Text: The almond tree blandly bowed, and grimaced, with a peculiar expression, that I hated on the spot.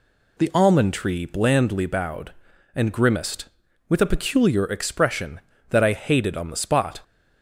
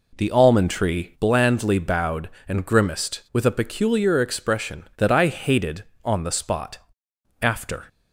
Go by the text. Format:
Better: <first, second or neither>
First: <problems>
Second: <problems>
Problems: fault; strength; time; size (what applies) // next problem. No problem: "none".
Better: first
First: none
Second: goes on to say "After"; slight; from 7.4 s on; 0.44 s long